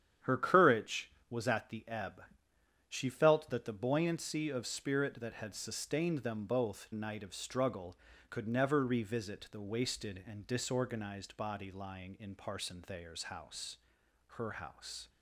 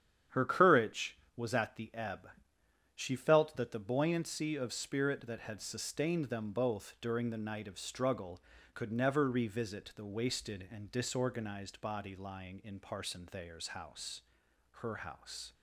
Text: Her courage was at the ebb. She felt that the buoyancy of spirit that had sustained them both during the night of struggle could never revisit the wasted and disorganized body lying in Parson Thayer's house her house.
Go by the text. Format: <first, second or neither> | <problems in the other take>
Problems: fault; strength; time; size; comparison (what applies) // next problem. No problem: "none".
second | starts louder than the rest; strong; until 1.4 s; 9.5 dB; strong in the second // skips "during the"; at 6.9 s // pauses between "house" and "her"; noticeable; at 13.7 s; 0.62 s long; noticeable in the second